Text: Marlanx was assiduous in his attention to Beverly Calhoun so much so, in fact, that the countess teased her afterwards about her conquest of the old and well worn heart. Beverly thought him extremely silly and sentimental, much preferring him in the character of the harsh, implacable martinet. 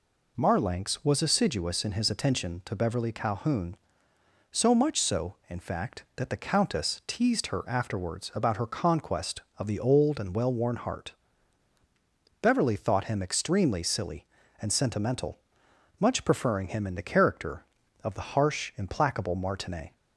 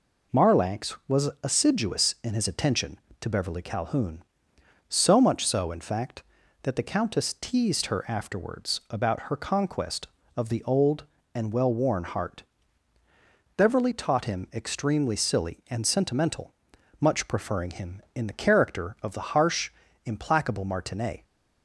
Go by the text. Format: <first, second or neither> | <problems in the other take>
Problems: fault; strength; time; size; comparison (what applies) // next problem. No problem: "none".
first | says "taught" for "thought"; at 13.9 s